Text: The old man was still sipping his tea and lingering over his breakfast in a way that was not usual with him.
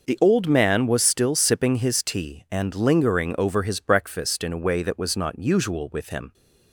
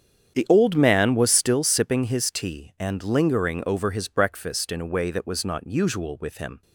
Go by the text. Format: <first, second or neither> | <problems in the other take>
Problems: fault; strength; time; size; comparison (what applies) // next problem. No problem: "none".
first | starts louder than the rest; strong; until 1.8 s; 8.5 dB